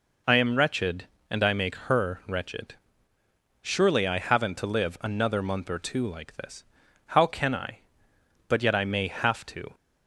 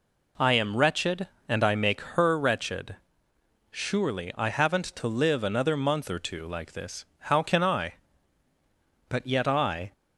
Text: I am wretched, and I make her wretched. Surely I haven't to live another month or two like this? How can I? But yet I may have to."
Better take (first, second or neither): first